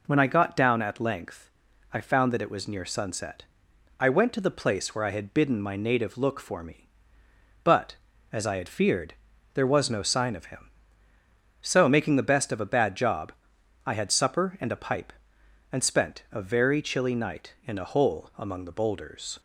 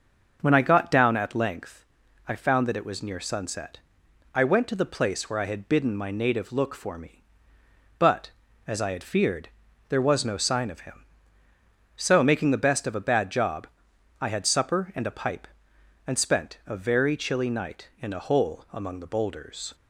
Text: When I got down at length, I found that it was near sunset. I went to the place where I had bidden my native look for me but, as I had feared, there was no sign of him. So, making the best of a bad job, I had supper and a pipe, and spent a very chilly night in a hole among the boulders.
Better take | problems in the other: first | starts louder than the rest; noticeable; until 1.6 s; 6 dB

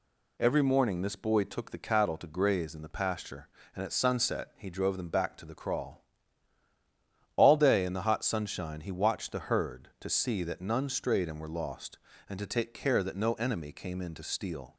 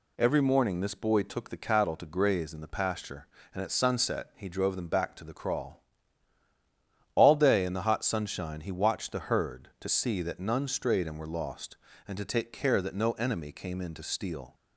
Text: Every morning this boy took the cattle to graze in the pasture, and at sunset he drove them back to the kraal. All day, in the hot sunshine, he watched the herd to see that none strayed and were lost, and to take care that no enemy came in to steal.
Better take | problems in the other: neither | none

